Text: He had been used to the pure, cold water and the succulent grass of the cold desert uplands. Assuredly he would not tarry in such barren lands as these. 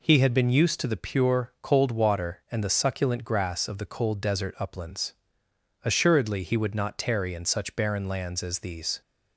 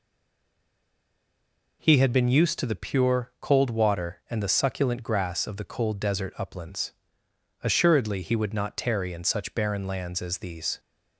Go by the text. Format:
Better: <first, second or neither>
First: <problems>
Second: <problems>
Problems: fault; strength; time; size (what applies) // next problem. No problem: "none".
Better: first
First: none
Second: stays silent before the first word; noticeable; until 1.8 s; 1.8 s long